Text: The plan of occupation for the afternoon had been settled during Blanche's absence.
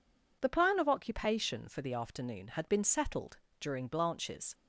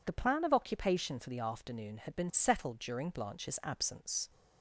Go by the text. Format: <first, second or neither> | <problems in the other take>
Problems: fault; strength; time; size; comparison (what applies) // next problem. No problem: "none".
second | pauses between "settled" and "during"; slight; at 3.3 s; 0.20 s long // stops before "absence"; at 4.5 s